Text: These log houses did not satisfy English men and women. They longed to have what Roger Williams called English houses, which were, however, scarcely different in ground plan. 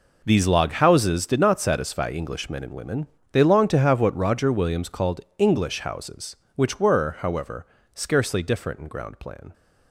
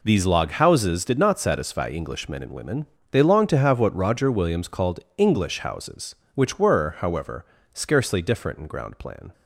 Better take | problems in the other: second | gets quieter; strong; throughout; 12.5 dB // pauses between "called" and "English"; slight; at 5.2 s; 0.16 s long; slight in the second

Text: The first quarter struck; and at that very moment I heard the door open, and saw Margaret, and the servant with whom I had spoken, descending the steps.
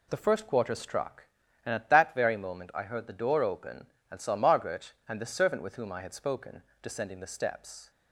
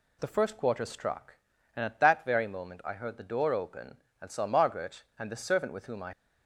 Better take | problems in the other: first | stops before "had spoken descending the steps"; at 6.1 s

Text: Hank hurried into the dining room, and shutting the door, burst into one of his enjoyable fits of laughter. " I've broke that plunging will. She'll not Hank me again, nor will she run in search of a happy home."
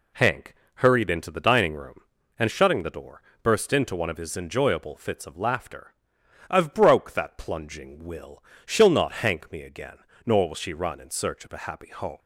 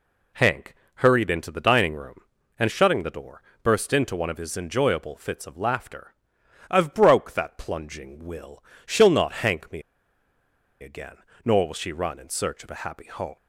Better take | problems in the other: first | pauses between "Hank" and "hurried"; slight; at 0.7 s; 0.22 s long; slight in the first // pauses between "me" and "again"; at 9.8 s; 1.0 s long

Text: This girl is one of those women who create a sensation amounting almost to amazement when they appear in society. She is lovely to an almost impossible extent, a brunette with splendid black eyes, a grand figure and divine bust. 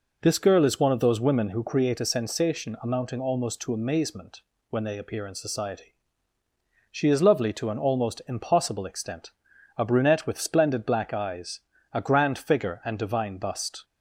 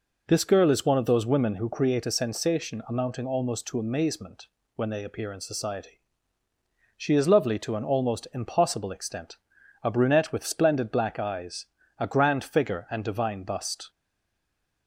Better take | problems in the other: first | pauses between "amazement" and "when"; slight; at 4.4 s; 0.28 s long; slight in the first // stays silent after the last word; slight; from 13.8 s on; 1.0 s long

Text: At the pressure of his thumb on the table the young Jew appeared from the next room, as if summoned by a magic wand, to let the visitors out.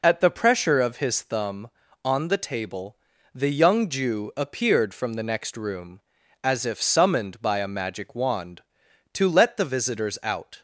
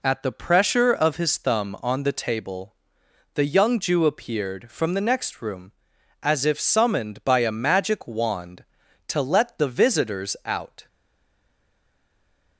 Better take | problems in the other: first | pauses between "table" and "the"; noticeable; at 2.7 s; 0.62 s long; also in the first // stays silent after the last word; noticeable; from 10.8 s on; 1.7 s long

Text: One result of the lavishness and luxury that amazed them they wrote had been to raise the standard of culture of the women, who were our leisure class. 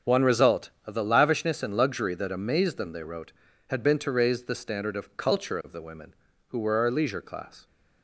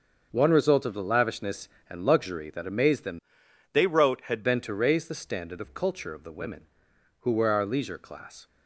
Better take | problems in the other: first | starts louder than the rest; until 1.3 s; 6.5 dB; also in the first // changes voice from "they" to "had"; from 3.7 to 4.4 s; 0.7 s long

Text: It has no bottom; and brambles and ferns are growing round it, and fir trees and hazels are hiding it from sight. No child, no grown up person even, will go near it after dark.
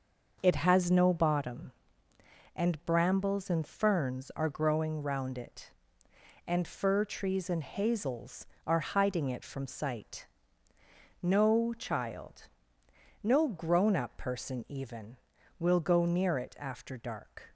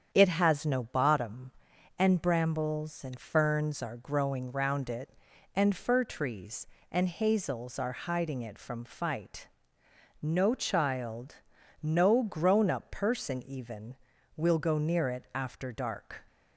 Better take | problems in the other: first | starts louder than the rest; strong; until 1.1 s; 8 dB; noticeable in the first // says "fight" for "sight"; at 8.8 s

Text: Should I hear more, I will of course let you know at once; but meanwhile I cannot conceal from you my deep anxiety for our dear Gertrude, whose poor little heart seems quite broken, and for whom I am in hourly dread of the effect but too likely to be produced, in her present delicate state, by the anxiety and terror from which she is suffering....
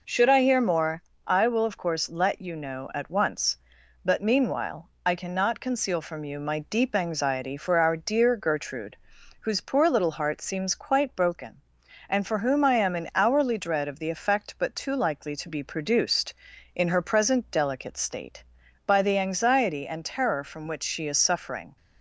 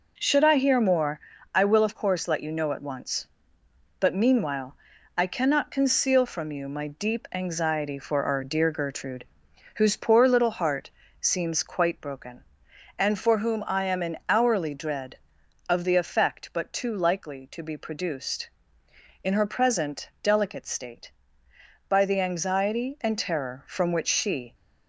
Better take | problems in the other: first | pauses between "meanwhile" and "I"; at 4.7 s; 0.40 s long // pauses between "heart" and "seems"; slight; at 10.8 s; 0.30 s long // stops before "is suffering"; at 24.5 s

